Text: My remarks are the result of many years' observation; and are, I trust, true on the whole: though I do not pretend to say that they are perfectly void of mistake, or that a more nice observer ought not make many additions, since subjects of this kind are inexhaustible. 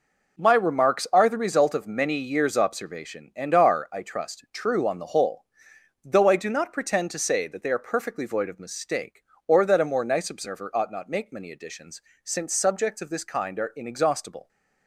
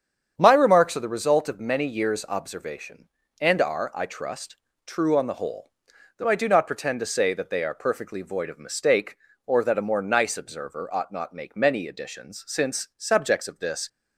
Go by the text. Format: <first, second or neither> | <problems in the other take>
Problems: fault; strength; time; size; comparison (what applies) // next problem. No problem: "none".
first | starts louder than the rest; strong; until 1.3 s; 8 dB // stops before "kind are inexhaustible"; at 13.8 s